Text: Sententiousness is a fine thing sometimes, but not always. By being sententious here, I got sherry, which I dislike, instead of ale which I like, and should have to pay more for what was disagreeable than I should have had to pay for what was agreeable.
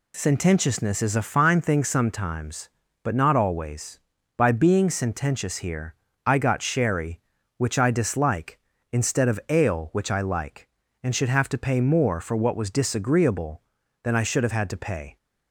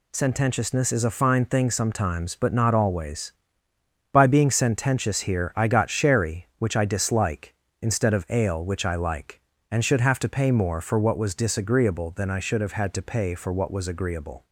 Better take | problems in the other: second | stops before "for what was agreeable"; at 15.1 s

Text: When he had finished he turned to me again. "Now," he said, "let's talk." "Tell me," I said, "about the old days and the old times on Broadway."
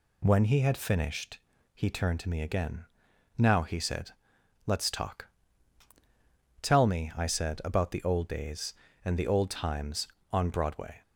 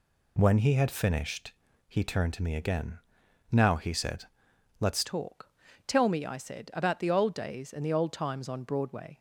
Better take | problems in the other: first | pauses between "finished" and "he"; slight; at 1.5 s; 0.36 s long; slight in the first // changes voice at "talk"; from 5.0 s on; 4.1 s long

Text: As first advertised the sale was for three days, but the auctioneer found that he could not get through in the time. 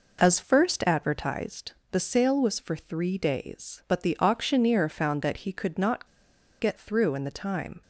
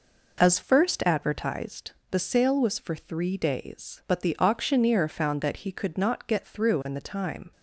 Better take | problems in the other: second | pauses between "advertised" and "the"; slight; at 1.7 s; 0.20 s long; slight in the second // pauses between "not" and "get"; noticeable; at 6.0 s; 0.54 s long

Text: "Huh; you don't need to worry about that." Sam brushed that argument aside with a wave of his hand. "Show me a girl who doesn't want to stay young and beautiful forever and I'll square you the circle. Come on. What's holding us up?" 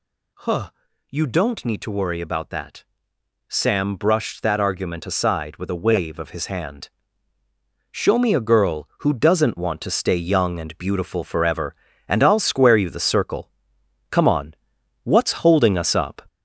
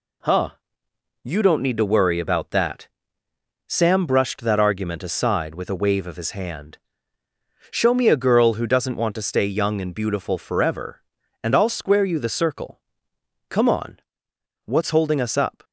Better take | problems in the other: second | gets louder; noticeable; throughout; 4 dB

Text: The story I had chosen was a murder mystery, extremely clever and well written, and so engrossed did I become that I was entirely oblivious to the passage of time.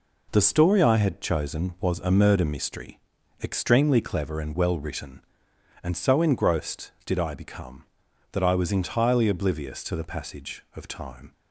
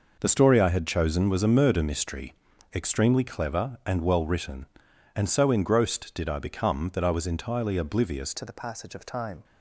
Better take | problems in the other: first | changes voice at "to"; from 8.3 s on; 1.1 s long

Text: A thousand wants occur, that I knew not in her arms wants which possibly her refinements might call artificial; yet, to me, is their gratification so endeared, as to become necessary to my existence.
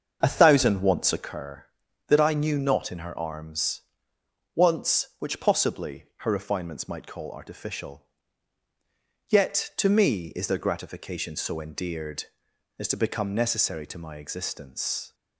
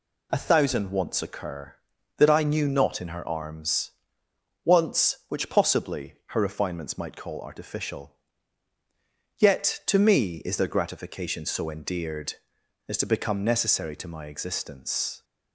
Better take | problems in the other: second | starts louder than the rest; until 1.4 s; 6.5 dB // pauses between "arms" and "wants"; noticeable; at 3.8 s; 0.72 s long; noticeable in the second

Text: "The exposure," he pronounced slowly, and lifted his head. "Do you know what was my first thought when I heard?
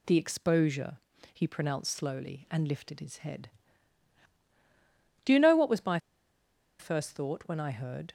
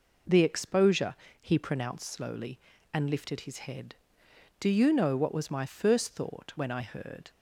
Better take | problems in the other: second | pauses between "my" and "first"; noticeable; at 5.9 s; 0.81 s long

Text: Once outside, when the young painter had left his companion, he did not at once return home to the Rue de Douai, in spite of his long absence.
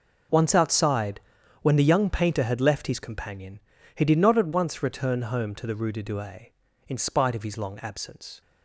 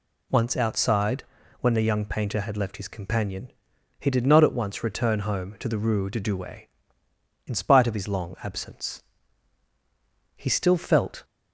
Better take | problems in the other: first | goes on to say "He still felt"; noticeable; from 10.3 s on; 0.88 s long

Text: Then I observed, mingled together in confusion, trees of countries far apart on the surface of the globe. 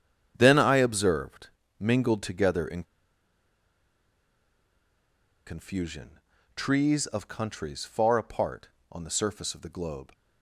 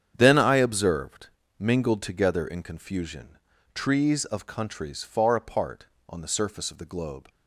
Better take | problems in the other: second | starts louder than the rest; strong; until 1.3 s; 8.5 dB; strong in the second // pauses between "in" and "confusion"; strong; at 2.8 s; 2.6 s long

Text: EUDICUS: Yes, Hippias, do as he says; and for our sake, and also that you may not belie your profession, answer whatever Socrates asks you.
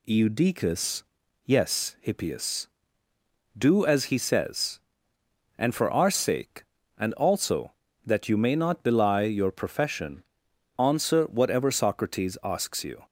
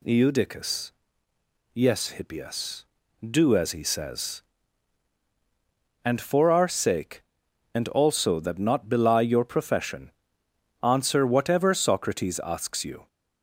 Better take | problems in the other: first | skips "you may"; at 8.5 s

